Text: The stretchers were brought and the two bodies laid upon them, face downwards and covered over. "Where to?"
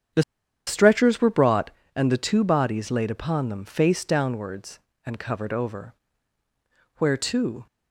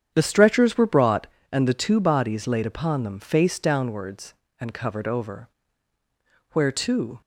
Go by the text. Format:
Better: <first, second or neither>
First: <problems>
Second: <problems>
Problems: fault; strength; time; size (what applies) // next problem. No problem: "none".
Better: second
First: starts louder than the rest; strong; until 1.5 s; 8.5 dB // pauses between "The" and "stretchers"; at 0.2 s; 0.44 s long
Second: starts louder than the rest; strong; until 1.1 s; 8.5 dB